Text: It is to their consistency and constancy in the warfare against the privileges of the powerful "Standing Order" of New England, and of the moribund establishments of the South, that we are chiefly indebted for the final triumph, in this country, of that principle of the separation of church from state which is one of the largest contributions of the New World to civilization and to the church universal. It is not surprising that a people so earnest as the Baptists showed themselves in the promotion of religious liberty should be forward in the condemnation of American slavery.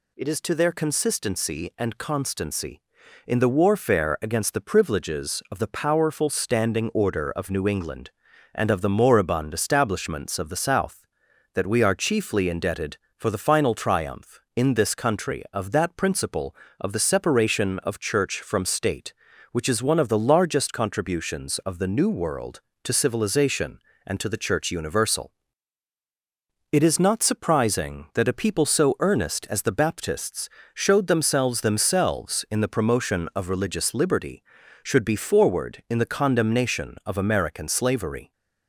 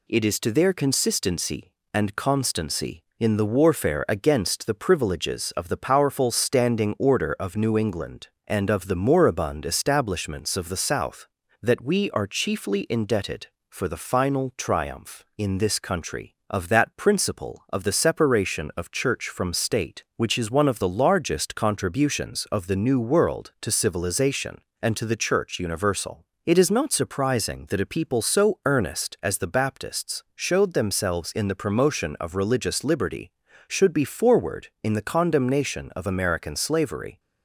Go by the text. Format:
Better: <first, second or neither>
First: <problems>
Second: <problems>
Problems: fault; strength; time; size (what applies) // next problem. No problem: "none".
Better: second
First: pauses between "Baptists" and "showed"; slight; at 30.4 s; 0.24 s long // says "themselves" twice; at 31.5 s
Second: none